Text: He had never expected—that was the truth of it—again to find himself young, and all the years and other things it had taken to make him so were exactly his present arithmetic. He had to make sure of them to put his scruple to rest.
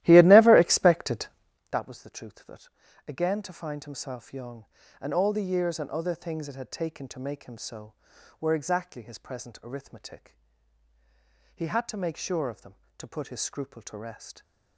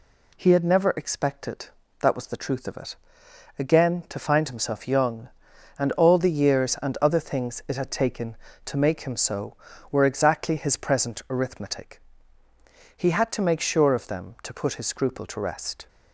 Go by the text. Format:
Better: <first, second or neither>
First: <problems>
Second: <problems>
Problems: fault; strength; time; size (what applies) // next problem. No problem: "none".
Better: second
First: starts louder than the rest; strong; until 1.7 s; 15 dB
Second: none